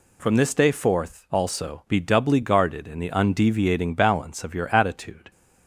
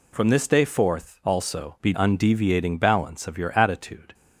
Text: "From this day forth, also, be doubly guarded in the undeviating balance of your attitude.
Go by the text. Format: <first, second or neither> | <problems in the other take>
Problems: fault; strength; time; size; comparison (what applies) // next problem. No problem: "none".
first | skips "doubly guarded in the"; at 1.9 s